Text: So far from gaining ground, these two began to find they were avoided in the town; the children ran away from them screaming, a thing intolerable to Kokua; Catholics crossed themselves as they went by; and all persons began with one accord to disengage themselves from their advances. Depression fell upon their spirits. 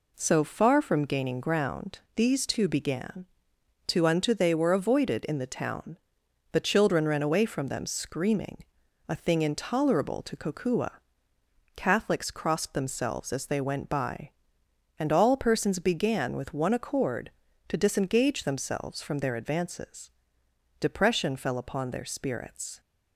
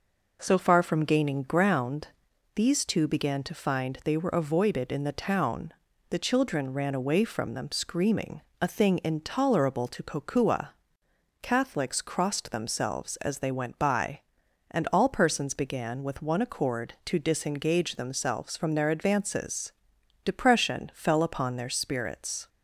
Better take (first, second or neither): second